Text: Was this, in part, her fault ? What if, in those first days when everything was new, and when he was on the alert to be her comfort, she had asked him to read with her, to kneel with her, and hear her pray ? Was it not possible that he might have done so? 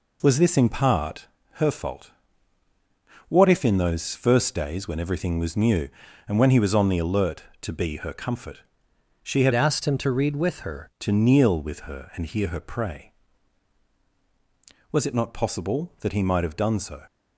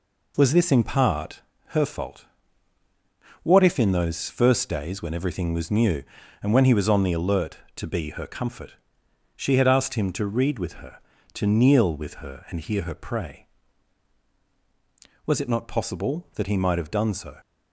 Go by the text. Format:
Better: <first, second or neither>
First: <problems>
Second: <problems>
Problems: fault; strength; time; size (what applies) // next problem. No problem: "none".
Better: second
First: changes voice from "asked" to "her"; from 9.5 to 10.8 s; 1.3 s long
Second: none